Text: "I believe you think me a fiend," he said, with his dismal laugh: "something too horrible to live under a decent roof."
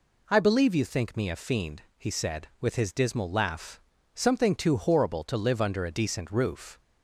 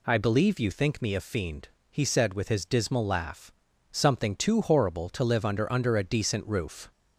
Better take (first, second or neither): first